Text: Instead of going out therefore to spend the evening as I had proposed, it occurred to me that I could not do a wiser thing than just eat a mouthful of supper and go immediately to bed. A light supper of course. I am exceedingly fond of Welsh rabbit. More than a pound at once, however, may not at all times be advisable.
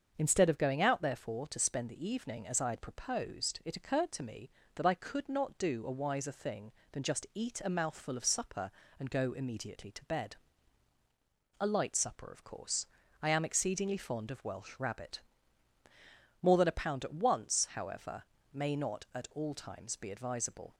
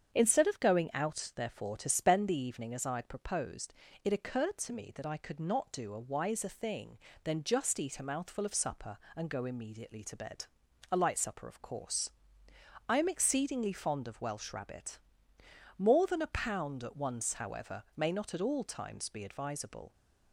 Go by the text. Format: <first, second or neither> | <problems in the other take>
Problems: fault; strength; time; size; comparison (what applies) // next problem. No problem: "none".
neither | starts louder than the rest; the same in both